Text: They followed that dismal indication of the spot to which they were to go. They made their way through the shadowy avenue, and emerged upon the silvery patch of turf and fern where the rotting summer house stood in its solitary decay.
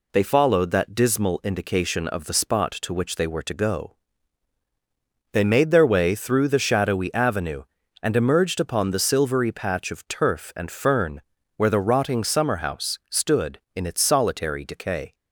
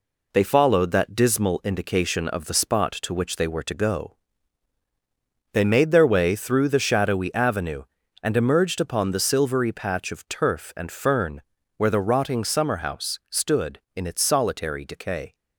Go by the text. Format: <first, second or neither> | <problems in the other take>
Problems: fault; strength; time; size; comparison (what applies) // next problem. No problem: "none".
first | gets quieter; noticeable; throughout; 5 dB // pauses between "fern" and "where"; at 11.4 s; 0.38 s long; also in the first